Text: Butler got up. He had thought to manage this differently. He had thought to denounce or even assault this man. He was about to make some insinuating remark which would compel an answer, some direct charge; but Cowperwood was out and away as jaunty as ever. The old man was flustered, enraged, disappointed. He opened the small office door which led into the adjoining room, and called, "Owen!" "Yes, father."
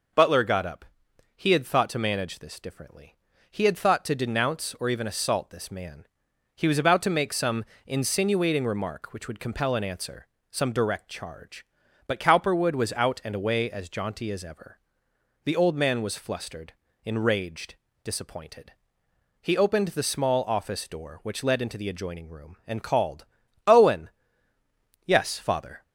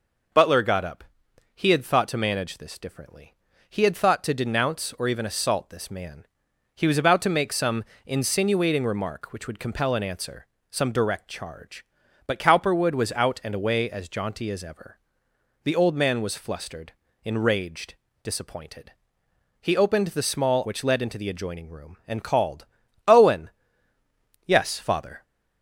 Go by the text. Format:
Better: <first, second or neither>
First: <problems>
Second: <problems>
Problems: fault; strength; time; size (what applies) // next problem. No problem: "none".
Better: first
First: pauses between "some" and "insinuating"; slight; at 7.6 s; 0.22 s long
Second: pauses between "some" and "insinuating"; slight; at 7.8 s; 0.22 s long // skips "office door"; at 20.6 s